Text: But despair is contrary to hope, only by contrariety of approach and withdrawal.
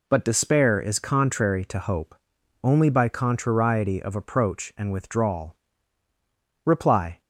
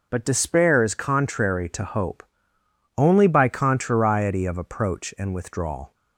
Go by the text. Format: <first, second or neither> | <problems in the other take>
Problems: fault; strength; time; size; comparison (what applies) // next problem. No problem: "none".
second | goes on to say "Reply"; from 6.6 s on; 0.56 s long